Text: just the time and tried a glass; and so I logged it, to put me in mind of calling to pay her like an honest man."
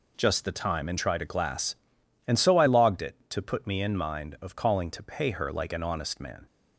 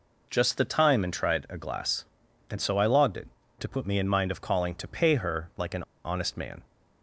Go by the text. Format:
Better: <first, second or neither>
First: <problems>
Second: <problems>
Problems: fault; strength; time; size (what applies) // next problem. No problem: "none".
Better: first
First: none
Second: pauses between "an" and "honest"; slight; at 5.8 s; 0.22 s long